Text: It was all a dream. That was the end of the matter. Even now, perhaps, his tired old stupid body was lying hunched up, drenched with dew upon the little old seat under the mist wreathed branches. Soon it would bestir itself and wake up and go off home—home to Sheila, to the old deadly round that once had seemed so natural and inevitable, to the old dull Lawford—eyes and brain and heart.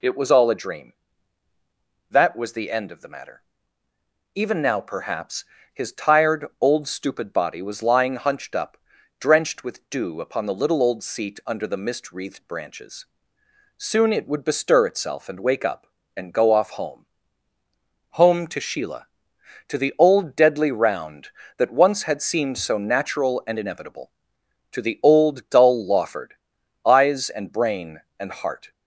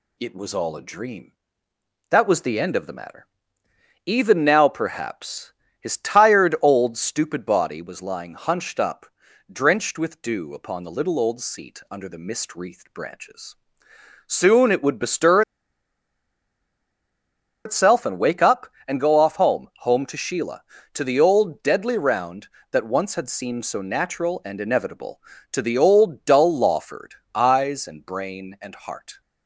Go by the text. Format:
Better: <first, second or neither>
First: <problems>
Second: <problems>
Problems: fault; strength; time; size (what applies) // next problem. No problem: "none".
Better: first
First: none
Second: pauses between "bestir" and "itself"; strong; at 15.4 s; 2.2 s long